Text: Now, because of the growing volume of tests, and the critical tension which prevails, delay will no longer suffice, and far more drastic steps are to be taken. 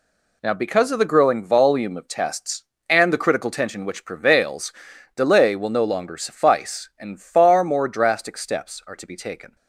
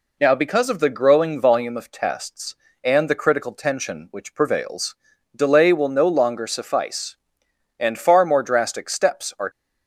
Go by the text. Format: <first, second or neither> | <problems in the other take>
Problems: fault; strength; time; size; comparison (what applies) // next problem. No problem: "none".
first | stops before "to be taken"; at 9.4 s